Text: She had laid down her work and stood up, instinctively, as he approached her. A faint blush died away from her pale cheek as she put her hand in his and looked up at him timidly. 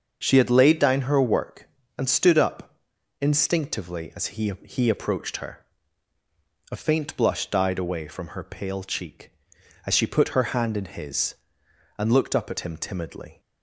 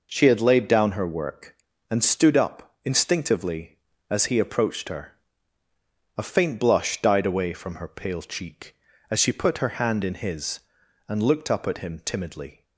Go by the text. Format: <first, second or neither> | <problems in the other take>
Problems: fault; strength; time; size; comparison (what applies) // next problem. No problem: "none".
second | starts louder than the rest; until 1.2 s; 6.5 dB // says "he" twice; at 4.6 s